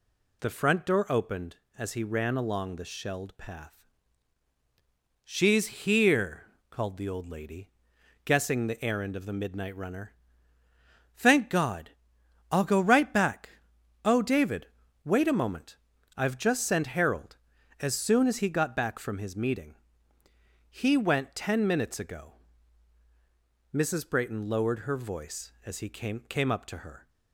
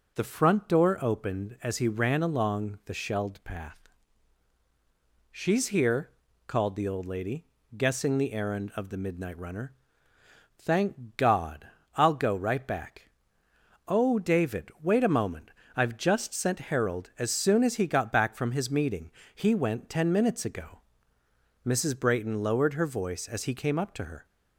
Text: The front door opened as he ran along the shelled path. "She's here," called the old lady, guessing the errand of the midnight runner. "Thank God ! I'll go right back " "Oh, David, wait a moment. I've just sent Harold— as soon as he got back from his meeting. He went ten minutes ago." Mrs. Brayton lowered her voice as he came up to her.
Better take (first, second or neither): second